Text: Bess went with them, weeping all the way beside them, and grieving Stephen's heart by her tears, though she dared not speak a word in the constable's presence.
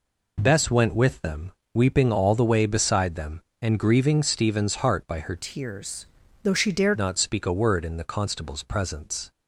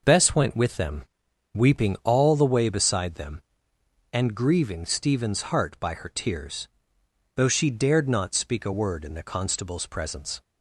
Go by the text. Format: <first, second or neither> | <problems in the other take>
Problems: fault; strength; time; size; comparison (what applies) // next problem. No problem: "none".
second | changes voice from "tears" to "dared"; from 5.3 to 6.9 s; 1.6 s long